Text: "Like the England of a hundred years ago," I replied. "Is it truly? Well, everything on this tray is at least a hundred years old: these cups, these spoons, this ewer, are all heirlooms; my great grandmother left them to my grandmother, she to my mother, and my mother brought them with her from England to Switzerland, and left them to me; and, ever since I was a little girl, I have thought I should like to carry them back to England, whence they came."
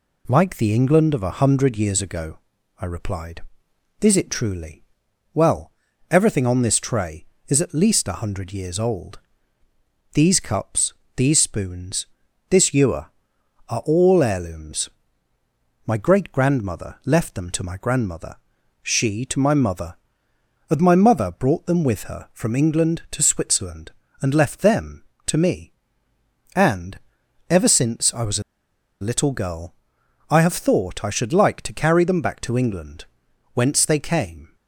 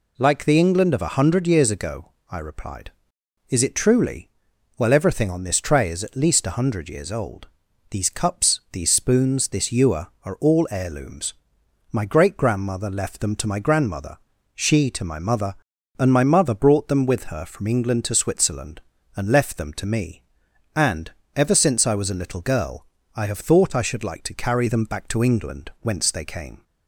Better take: second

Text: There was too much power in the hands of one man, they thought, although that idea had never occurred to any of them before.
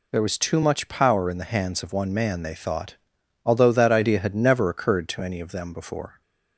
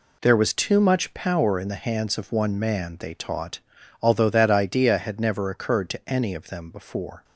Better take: first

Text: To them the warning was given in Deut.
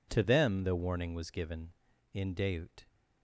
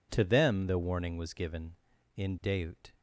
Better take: neither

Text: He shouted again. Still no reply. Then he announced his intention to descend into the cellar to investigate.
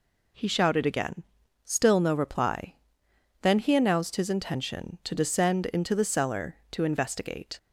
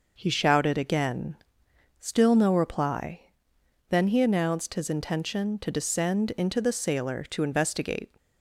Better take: first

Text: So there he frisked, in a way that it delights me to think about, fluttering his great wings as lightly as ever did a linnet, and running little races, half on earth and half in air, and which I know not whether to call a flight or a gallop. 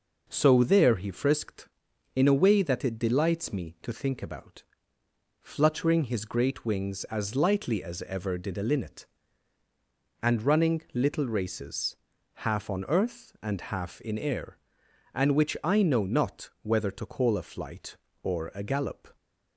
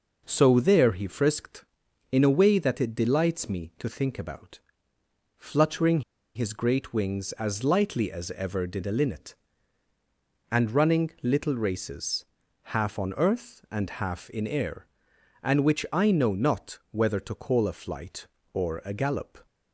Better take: first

